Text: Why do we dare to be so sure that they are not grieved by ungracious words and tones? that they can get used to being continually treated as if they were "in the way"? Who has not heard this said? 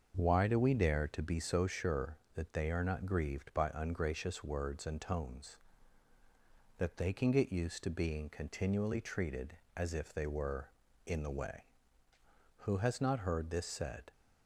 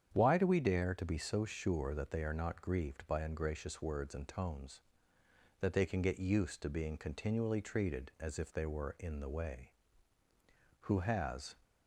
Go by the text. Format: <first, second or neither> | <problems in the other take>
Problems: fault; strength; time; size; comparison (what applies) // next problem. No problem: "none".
first | starts louder than the rest; strong; until 1.1 s; 8.5 dB; also in the first // stops before "not heard this said"; at 11.6 s